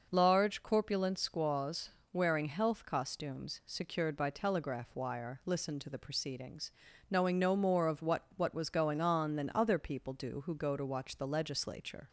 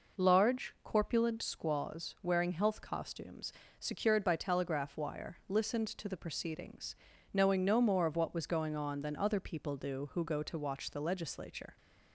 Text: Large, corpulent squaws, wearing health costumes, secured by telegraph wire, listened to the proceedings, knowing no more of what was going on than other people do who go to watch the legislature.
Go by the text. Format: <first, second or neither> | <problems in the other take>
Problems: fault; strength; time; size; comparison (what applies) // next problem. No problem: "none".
second | says "what" twice; at 8.3 s